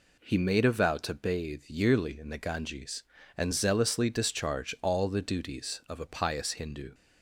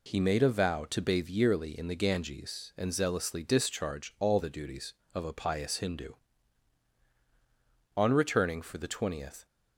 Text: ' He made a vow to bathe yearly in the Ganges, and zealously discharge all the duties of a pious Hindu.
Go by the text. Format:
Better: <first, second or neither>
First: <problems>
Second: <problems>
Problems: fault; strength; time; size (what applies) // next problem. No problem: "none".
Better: first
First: none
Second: goes on to say "On returning for the twentieth"; from 7.9 s on; 1.4 s long